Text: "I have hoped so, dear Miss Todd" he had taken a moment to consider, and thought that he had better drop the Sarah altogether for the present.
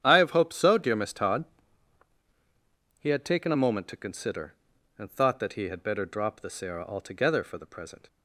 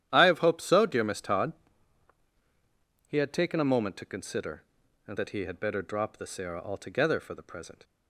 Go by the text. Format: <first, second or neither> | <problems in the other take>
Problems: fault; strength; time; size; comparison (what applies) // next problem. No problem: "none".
first | starts louder than the rest; strong; until 1.1 s; 11 dB; strong in the first // pauses between "Todd" and "he"; strong; at 1.5 s; 1.5 s long; strong in the first // skips "thought"; at 5.1 s